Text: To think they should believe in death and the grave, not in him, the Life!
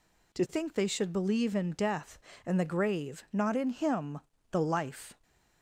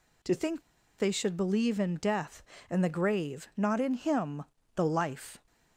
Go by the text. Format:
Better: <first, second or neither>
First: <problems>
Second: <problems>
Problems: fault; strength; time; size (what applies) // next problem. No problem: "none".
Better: first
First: none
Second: pauses between "think" and "they"; at 0.6 s; 0.38 s long